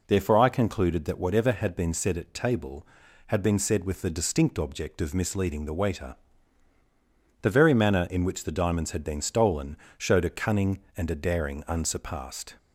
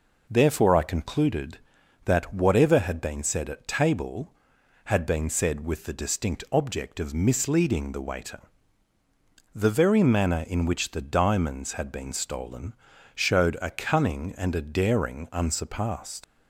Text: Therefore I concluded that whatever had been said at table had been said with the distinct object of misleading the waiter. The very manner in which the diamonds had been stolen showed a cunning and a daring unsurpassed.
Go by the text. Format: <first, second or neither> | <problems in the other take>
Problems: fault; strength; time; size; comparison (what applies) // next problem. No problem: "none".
first | pauses between "stolen" and "showed"; at 12.7 s; 0.42 s long; slight in the first // leaves "unsurpassed" unfinished; at 16.2 s; 70 ms